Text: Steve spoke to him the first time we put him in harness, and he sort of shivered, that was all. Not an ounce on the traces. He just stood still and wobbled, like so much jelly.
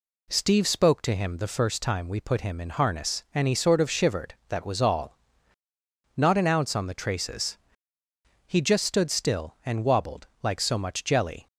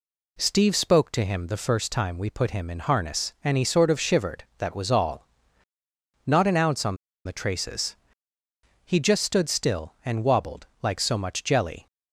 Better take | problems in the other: first | pauses between "on" and "the"; slight; at 6.9 s; 0.29 s long

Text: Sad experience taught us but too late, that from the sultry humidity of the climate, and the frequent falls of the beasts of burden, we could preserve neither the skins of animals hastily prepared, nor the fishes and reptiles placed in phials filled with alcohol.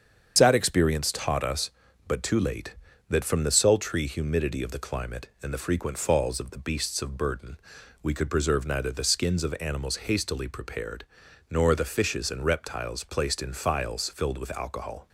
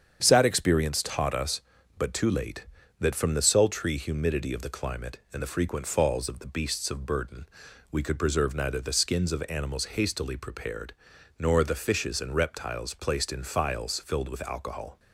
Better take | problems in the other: second | loses the start of "Sad"; at 0.3 s; 65 ms // starts louder than the rest; strong; until 1.3 s; 7.5 dB; strong in the second

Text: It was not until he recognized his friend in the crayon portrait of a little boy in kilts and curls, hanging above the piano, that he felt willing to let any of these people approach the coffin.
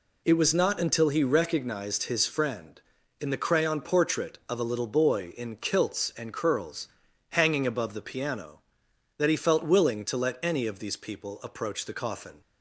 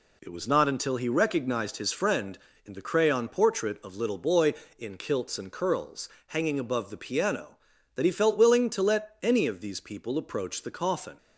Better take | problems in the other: first | skips "a"; at 3.9 s

